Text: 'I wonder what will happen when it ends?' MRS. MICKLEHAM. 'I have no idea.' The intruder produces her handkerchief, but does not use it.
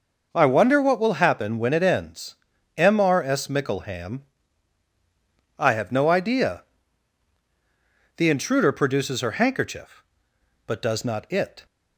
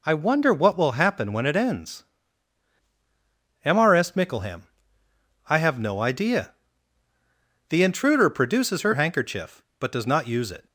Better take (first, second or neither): second